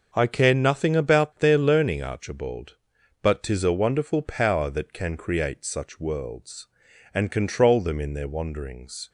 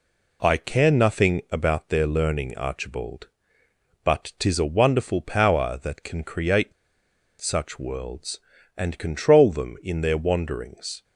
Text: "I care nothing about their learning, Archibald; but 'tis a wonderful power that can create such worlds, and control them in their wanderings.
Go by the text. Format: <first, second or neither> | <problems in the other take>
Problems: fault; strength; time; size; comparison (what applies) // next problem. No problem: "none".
first | pauses between "create" and "such"; noticeable; at 6.7 s; 0.68 s long